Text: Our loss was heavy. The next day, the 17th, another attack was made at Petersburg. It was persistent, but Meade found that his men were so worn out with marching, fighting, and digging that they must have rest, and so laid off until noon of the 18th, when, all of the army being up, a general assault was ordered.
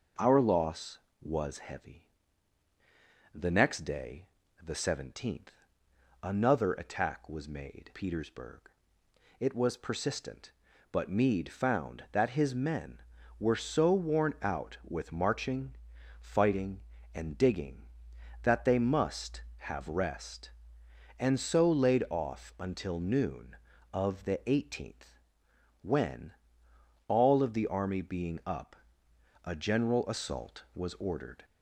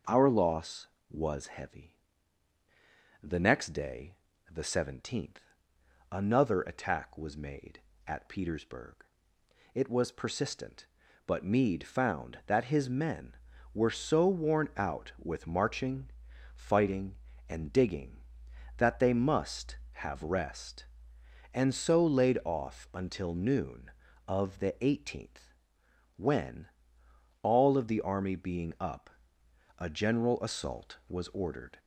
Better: second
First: skips "at"; at 7.9 s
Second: none

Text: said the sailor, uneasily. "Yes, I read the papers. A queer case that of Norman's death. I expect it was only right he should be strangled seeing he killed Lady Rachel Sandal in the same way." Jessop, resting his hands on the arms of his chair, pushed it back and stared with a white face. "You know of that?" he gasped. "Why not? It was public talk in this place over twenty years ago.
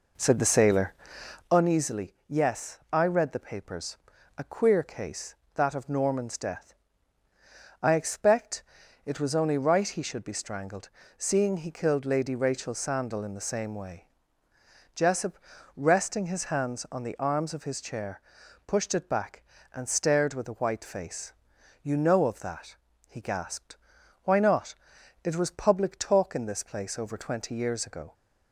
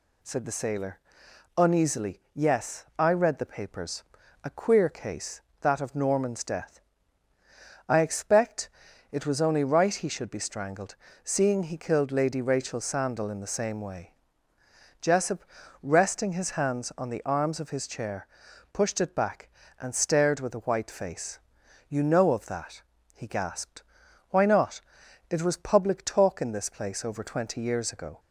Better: second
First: starts louder than the rest; noticeable; until 1.6 s; 4.5 dB // pauses between "expect" and "it"; at 8.6 s; 0.42 s long // pauses between "strangled" and "seeing"; slight; at 10.8 s; 0.28 s long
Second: pauses between "expect" and "it"; at 8.6 s; 0.42 s long // pauses between "strangled" and "seeing"; slight; at 10.9 s; 0.28 s long

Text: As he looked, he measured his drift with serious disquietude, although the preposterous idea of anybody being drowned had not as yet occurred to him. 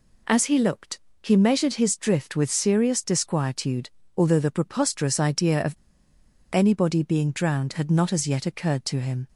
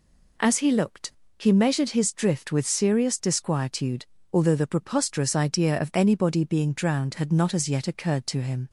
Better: second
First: pauses between "of" and "anybody"; noticeable; at 5.7 s; 0.76 s long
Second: none

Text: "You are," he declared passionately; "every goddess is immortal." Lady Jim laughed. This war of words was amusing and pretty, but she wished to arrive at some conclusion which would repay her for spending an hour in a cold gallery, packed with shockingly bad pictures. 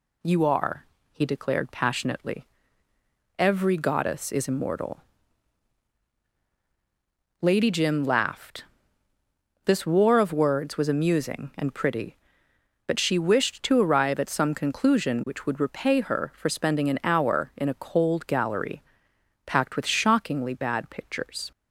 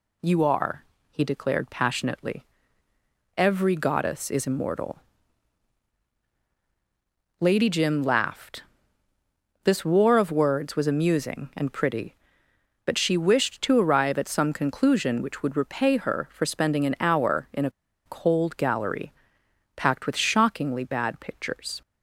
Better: first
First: none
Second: pauses between "a" and "cold"; at 17.6 s; 0.36 s long

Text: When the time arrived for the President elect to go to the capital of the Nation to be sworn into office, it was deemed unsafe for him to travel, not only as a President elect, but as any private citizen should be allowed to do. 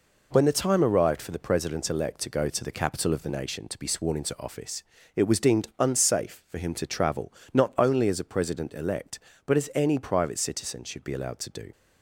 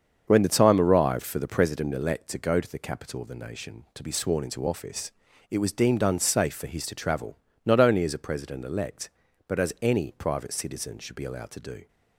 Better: first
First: none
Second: starts louder than the rest; until 1.2 s; 7 dB // says "his" for "him"; at 6.6 s

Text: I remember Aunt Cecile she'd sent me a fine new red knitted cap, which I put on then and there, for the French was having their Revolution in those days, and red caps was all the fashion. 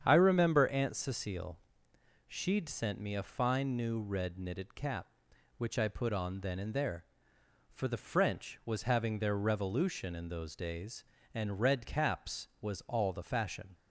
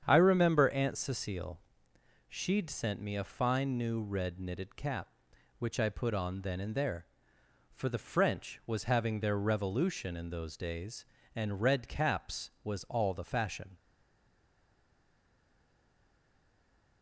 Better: first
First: starts louder than the rest; strong; until 1.0 s; 8 dB // pauses between "Cecile" and "she'd"; noticeable; at 1.5 s; 0.68 s long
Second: starts louder than the rest; strong; until 1.0 s; 8 dB // pauses between "Cecile" and "she'd"; noticeable; at 1.5 s; 0.68 s long // stays silent after the last word; strong; from 13.7 s on; 3.3 s long

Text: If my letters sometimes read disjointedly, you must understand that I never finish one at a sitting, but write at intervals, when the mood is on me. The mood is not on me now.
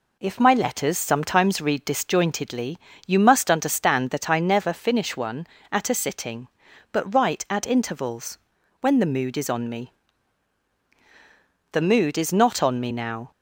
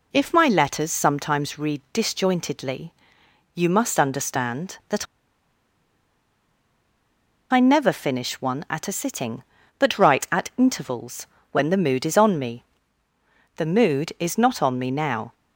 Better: first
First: none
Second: pauses between "that" and "I"; strong; at 5.0 s; 2.4 s long

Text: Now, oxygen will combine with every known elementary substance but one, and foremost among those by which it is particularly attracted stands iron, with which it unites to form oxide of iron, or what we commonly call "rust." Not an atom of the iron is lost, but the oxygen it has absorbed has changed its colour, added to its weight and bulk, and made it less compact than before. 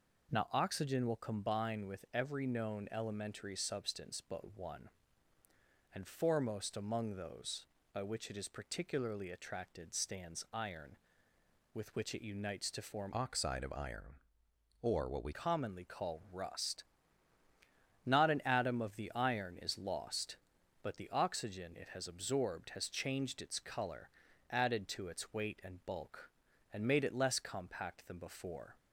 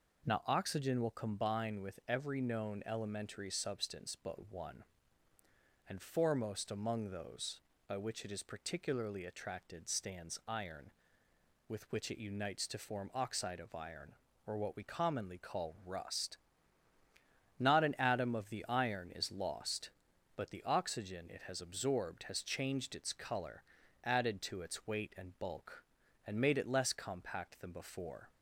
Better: second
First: changes voice from "oxide" to "we"; from 13.1 to 15.3 s; 2.2 s long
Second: none

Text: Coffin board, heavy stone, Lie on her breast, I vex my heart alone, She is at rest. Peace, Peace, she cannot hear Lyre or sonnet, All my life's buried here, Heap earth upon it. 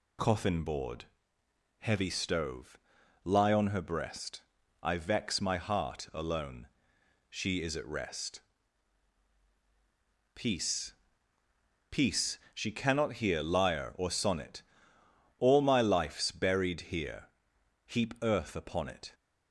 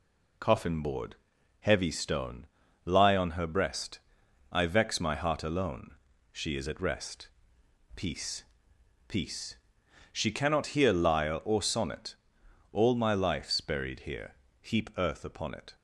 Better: second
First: says "stove" for "stone"; at 2.0 s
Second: none

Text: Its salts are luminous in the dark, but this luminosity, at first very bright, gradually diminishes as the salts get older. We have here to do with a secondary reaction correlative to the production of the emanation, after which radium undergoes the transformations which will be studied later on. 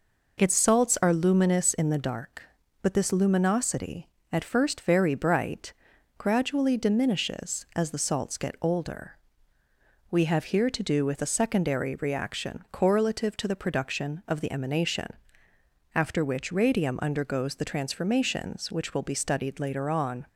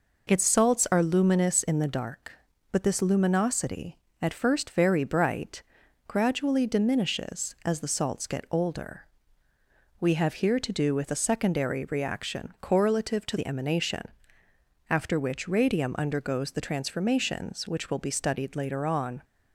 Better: first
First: none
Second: skips "the production of"; at 13.3 s

